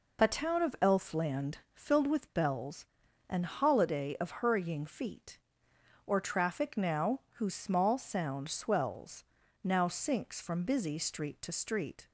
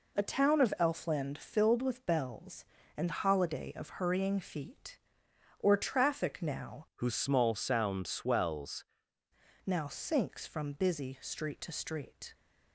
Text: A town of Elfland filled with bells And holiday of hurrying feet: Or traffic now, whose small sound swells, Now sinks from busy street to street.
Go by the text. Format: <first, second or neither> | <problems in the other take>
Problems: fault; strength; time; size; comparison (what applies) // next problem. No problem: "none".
first | changes voice from "whose" to "swells"; from 7.0 to 8.8 s; 1.8 s long